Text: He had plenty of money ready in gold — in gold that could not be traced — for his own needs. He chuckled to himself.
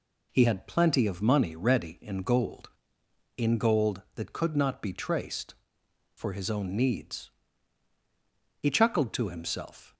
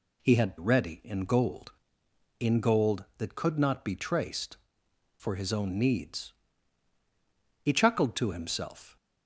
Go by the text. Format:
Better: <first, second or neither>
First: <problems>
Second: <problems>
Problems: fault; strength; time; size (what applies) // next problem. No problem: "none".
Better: first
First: none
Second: skips "plenty of money"; at 0.5 s